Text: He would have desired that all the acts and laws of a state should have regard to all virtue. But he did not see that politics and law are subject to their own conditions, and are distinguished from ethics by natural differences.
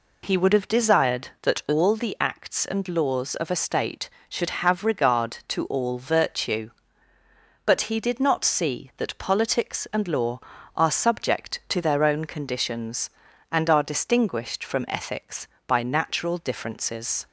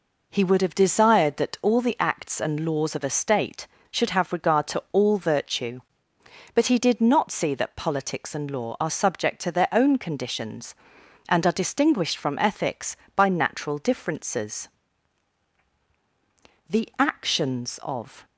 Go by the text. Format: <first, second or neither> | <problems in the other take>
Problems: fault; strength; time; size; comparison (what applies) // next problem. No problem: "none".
first | goes on to say "The actions of"; from 16.6 s on; 1.5 s long